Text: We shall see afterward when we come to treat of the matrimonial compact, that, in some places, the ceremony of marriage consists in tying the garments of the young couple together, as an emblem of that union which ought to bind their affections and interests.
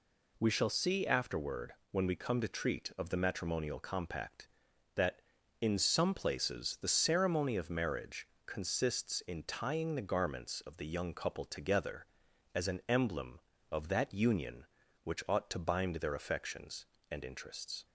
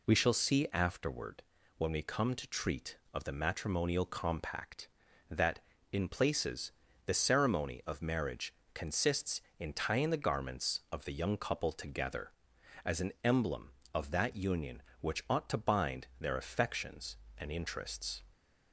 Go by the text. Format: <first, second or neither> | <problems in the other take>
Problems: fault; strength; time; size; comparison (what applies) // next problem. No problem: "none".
first | pauses between "afterward" and "when"; slight; at 1.4 s; 0.36 s long; slight in the first // skips "some"; at 6.0 s // pauses between "marriage" and "consists"; slight; at 8.5 s; 0.22 s long; slight in the first